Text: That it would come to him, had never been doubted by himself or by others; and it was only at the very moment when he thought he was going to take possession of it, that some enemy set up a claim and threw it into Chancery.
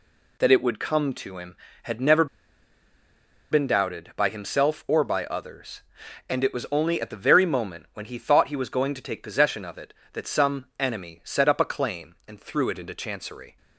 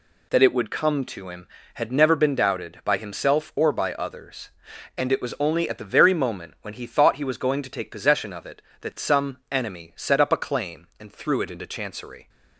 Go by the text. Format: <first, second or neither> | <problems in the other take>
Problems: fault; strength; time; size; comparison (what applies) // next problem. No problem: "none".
second | pauses between "never" and "been"; strong; at 2.2 s; 1.2 s long